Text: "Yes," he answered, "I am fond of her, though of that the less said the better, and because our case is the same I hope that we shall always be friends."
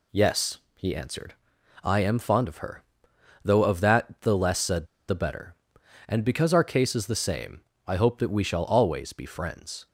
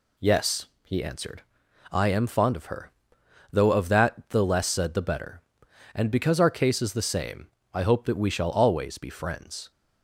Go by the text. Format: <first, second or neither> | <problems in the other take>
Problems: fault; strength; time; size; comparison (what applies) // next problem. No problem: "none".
second | pauses between "said" and "the"; slight; at 4.8 s; 0.23 s long // pauses between "same" and "I"; slight; at 7.6 s; 0.24 s long; slight in the second